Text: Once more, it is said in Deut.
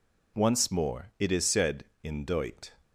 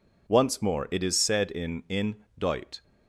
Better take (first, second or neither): first